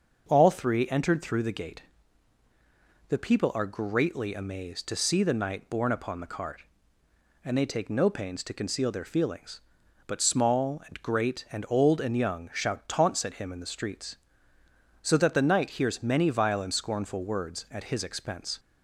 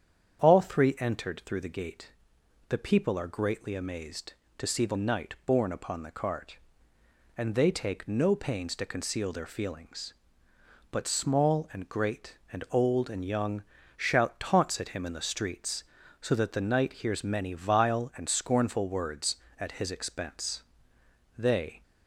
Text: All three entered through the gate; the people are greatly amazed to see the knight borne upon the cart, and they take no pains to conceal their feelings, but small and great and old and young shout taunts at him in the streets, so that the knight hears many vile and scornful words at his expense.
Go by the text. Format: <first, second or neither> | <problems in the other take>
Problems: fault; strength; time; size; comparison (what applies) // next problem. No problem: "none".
first | starts louder than the rest; strong; until 1.4 s; 8 dB; also in the first // pauses between "young" and "shout"; slight; at 13.6 s; 0.34 s long // goes on to say "They"; slight; from 21.3 s on; 0.46 s long